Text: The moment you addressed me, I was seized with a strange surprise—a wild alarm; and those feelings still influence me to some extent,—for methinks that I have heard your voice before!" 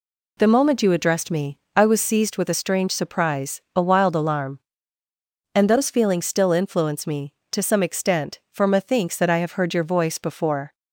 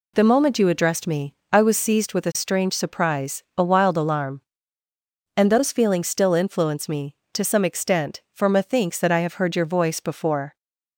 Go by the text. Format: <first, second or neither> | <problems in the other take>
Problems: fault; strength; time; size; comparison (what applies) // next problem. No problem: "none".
neither | none